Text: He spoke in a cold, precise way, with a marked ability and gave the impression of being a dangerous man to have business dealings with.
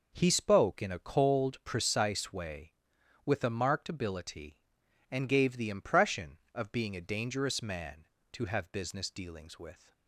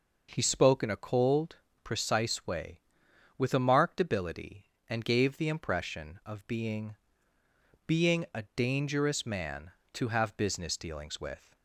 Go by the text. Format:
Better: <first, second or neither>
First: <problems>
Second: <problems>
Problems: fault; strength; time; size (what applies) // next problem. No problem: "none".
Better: first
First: none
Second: says "being" twice; at 7.8 s